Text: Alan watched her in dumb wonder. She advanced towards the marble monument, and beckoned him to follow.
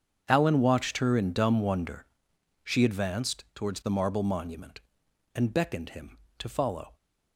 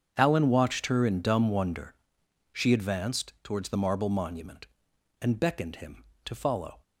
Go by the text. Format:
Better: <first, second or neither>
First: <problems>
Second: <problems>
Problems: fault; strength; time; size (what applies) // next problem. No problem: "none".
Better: neither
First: starts louder than the rest; strong; until 1.2 s; 7.5 dB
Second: starts louder than the rest; strong; until 1.1 s; 7.5 dB